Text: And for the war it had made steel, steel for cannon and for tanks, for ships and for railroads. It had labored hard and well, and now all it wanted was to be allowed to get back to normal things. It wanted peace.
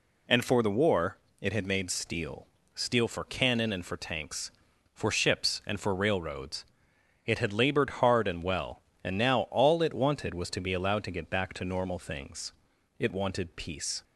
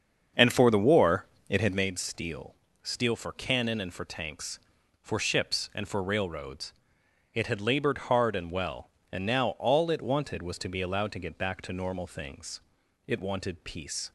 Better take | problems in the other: first | starts louder than the rest; until 1.9 s; 7 dB // pauses between "war" and "it"; slight; at 1.2 s; 0.22 s long; slight in the first

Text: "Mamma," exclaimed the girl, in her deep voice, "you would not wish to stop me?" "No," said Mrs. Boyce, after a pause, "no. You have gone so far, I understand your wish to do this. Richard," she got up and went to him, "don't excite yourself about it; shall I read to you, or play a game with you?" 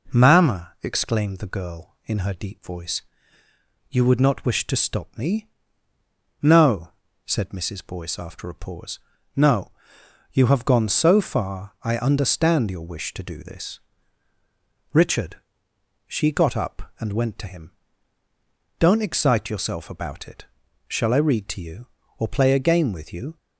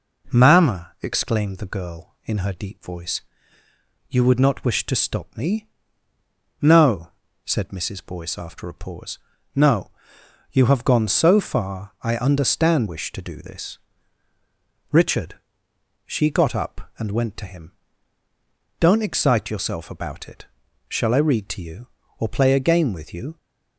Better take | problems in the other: first | skips "your"; at 12.8 s

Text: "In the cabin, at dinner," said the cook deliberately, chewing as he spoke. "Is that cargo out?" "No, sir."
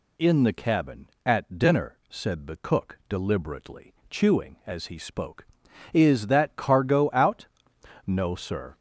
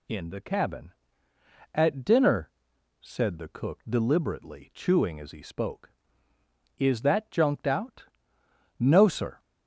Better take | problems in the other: first | says "junked" for "cargo"; at 7.3 s

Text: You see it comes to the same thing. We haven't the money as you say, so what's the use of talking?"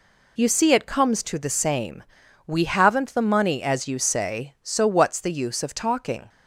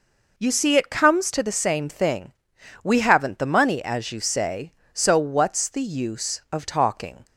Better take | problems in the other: second | skips "thing"; at 2.2 s

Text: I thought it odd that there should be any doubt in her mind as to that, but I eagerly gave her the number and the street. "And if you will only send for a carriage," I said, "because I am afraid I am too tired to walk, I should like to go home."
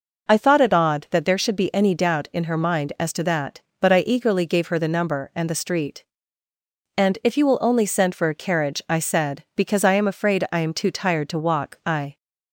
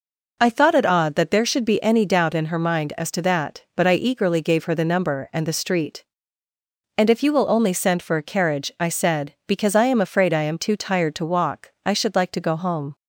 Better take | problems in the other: second | stops before "should like to go home"; at 12.1 s

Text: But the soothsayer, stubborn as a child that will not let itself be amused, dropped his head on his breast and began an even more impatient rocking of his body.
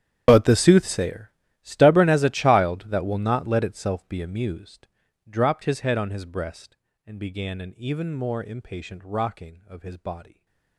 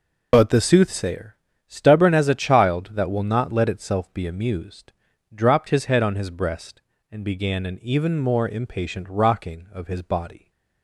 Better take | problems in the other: second | gets quieter; strong; throughout; 21 dB // stays silent after the last word; slight; from 10.2 s on; 0.5 s long

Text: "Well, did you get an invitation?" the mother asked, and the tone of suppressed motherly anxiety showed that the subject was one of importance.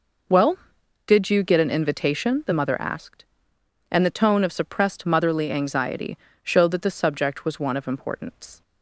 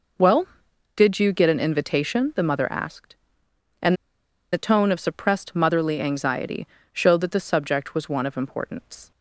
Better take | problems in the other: first | pauses between "and" and "the"; noticeable; at 3.9 s; 0.58 s long // pauses between "anxiety" and "showed"; slight; at 6.6 s; 0.26 s long; slight in the first

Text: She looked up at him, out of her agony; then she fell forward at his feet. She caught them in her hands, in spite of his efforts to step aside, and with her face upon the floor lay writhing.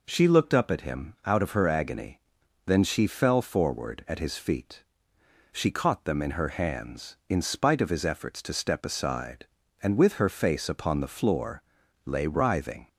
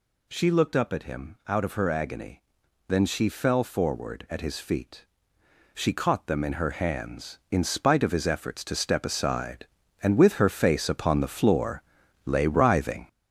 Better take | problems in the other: first | gets louder; throughout; 7 dB // pauses between "floor" and "lay"; at 11.8 s; 0.44 s long; also in the first

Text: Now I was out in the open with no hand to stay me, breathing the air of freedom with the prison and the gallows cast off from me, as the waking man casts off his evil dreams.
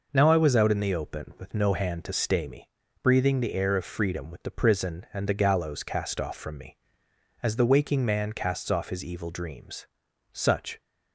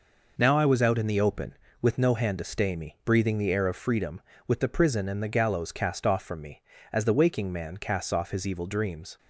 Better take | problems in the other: second | goes on to say "Such"; slight; from 10.3 s on; 0.48 s long

